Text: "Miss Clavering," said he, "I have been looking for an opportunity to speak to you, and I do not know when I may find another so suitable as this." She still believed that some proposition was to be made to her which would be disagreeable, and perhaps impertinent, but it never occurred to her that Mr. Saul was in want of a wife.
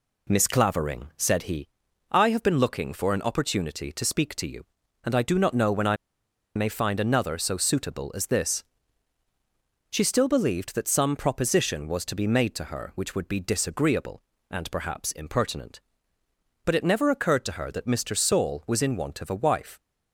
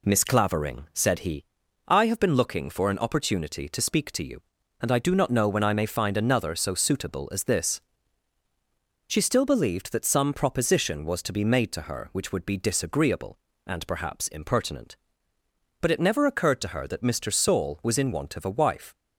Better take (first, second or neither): second